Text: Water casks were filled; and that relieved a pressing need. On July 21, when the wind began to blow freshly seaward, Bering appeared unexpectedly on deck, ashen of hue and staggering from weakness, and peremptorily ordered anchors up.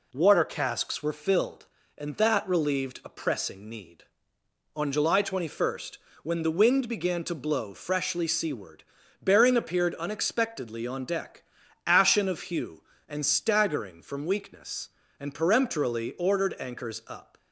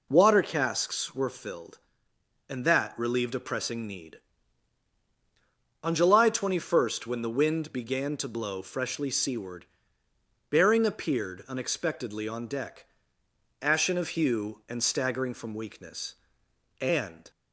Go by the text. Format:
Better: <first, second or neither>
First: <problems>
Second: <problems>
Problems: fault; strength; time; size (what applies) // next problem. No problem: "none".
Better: first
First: none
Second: stops before "peremptorily ordered anchors up"; at 17.3 s